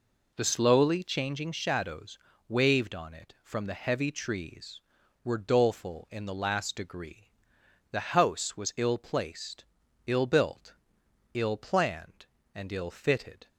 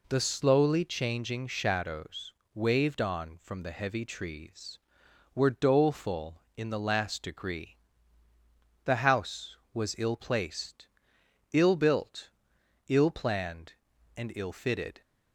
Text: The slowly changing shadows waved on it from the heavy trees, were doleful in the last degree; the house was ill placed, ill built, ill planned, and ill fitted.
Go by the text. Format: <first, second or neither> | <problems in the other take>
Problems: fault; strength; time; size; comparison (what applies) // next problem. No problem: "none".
first | pauses between "shadows" and "waved"; slight; at 2.3 s; 0.22 s long; slight in the first // skips "it"; at 3.3 s